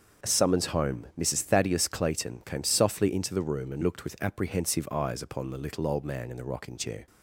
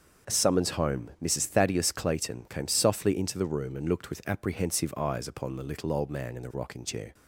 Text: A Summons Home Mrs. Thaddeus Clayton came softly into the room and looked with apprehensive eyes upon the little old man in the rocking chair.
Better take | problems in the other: neither | starts louder than the rest; the same in both

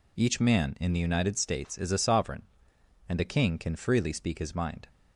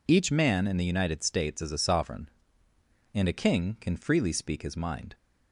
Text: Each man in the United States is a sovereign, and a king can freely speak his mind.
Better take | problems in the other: neither | none

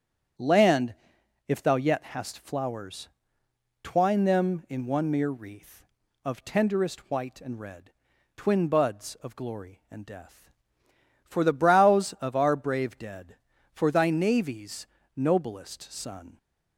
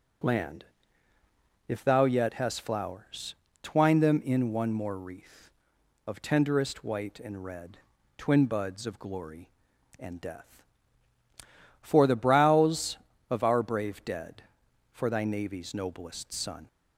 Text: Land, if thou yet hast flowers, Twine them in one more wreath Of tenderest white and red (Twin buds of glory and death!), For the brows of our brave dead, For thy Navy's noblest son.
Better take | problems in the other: second | starts louder than the rest; strong; until 1.9 s; 8 dB // says "mere" for "more"; at 5.1 s // pauses between "Navy's" and "noblest"; slight; at 14.8 s; 0.28 s long

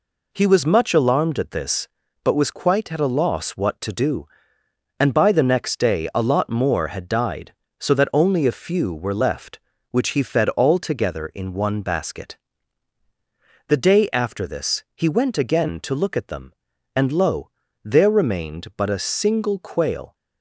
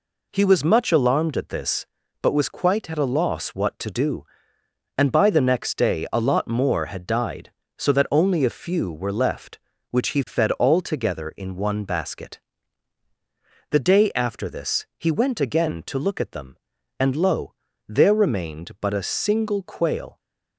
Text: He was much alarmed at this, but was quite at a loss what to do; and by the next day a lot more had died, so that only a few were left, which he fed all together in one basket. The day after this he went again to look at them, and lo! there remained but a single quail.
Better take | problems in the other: neither | none

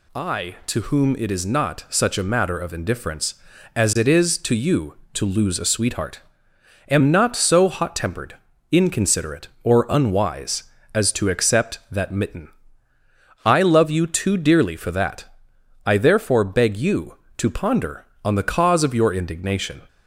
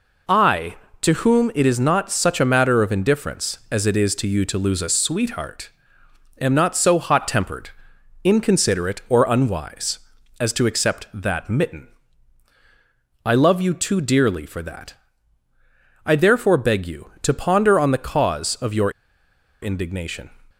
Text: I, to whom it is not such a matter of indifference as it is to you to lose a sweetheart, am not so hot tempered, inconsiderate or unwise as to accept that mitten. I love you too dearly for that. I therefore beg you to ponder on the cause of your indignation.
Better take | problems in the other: first | pauses between "your" and "indignation"; noticeable; at 18.9 s; 0.70 s long

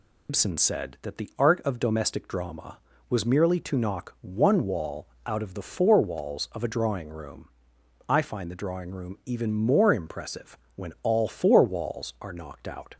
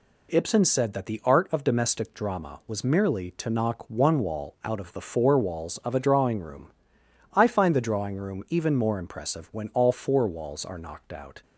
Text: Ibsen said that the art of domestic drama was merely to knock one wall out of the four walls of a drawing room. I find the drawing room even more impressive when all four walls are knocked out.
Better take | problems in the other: second | loses the start of "Ibsen"; at 0.2 s; 115 ms // pauses between "wall" and "out"; slight; at 5.0 s; 0.18 s long // pauses between "impressive" and "when"; slight; at 10.5 s; 0.18 s long

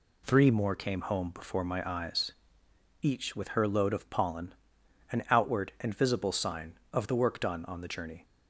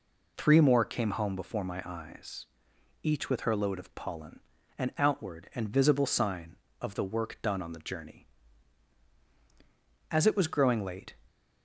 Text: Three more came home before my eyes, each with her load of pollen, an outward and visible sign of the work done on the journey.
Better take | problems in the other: first | goes on to say "As it was growing late"; noticeable; from 10.1 s on; 1.0 s long

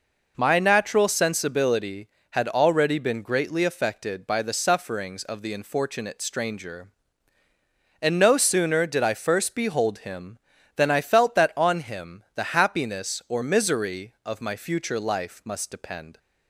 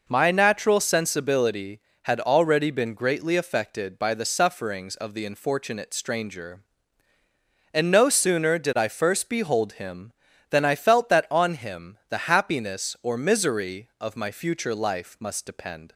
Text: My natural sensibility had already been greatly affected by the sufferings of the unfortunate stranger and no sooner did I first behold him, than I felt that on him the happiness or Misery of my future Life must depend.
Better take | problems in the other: neither | none

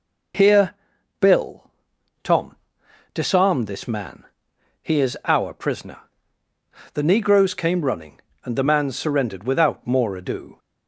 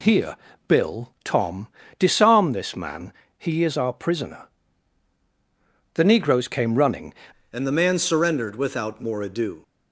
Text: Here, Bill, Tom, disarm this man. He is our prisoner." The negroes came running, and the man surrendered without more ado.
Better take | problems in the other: first | changes voice at "and"; from 7.5 s on; 2.1 s long

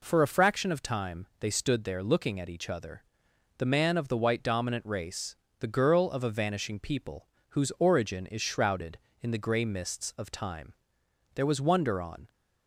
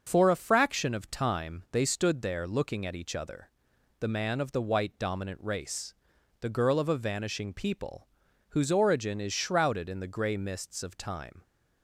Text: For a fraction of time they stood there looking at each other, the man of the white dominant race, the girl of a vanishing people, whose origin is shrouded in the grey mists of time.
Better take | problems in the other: second | goes on to say "There was wonder on"; noticeable; from 11.3 s on; 0.96 s long

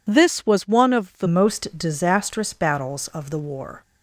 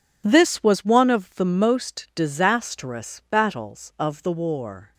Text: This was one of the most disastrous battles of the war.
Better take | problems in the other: second | changes voice at "most"; from 1.2 s on; 2.6 s long

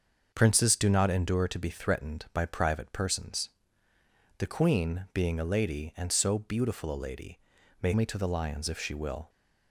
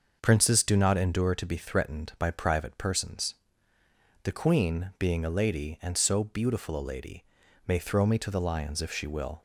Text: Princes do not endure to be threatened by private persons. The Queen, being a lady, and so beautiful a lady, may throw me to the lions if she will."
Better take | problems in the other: second | starts louder than the rest; until 1.3 s; 6.5 dB; noticeable in the second // skips "throw"; at 7.9 s

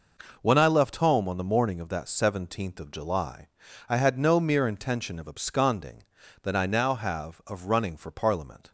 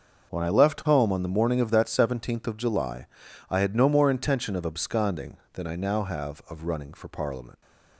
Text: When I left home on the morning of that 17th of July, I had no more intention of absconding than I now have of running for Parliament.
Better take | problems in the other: second | says "mere" for "more"; at 4.3 s

